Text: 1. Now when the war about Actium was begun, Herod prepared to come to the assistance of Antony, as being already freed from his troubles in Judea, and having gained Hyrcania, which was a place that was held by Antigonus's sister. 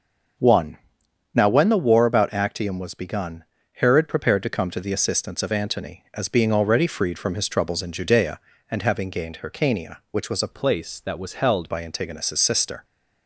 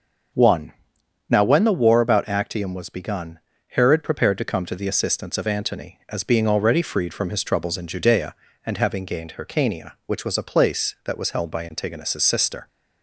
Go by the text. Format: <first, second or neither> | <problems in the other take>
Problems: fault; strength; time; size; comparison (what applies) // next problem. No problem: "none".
second | starts louder than the rest; noticeable; until 1.9 s; 6 dB; also in the second // changes voice from "place" to "held"; from 10.5 to 11.7 s; 1.2 s long